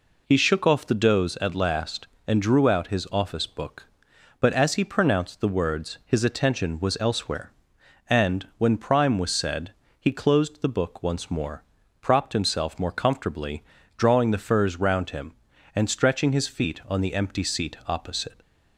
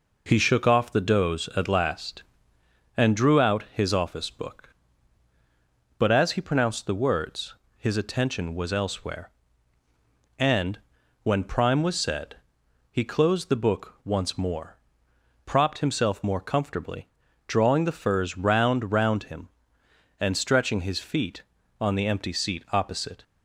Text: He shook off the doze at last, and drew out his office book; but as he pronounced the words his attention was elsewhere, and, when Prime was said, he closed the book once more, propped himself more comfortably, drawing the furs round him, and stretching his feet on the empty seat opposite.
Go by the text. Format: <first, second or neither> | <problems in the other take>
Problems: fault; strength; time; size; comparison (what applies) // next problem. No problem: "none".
first | pauses between "words" and "his"; slight; at 7.5 s; 0.24 s long // says "round" twice; at 18.9 s